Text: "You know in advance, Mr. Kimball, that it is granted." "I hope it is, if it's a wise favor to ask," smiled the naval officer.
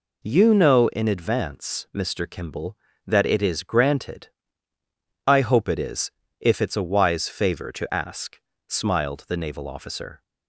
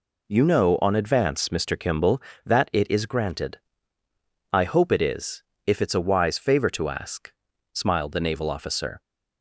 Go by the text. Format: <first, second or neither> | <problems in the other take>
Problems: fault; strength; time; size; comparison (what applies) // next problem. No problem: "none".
first | says "on" for "in"; at 0.8 s